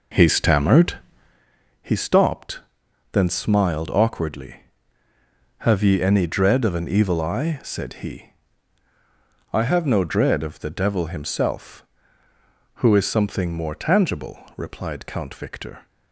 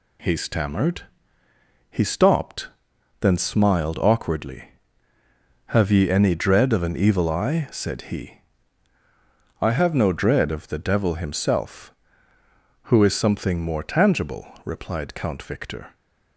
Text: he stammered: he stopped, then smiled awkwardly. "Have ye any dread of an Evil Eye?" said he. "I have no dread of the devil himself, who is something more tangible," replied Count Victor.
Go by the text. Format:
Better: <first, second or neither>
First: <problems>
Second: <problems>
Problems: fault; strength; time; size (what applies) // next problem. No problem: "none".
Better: second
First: starts louder than the rest; noticeable; until 1.5 s; 4.5 dB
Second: none